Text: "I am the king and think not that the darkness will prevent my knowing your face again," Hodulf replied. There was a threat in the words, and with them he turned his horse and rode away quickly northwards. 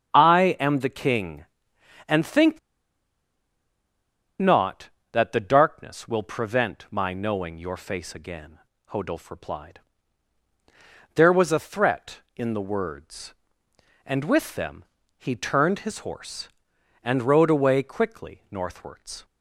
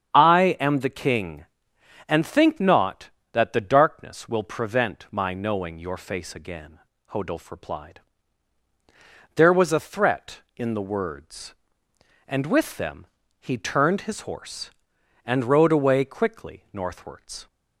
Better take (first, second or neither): second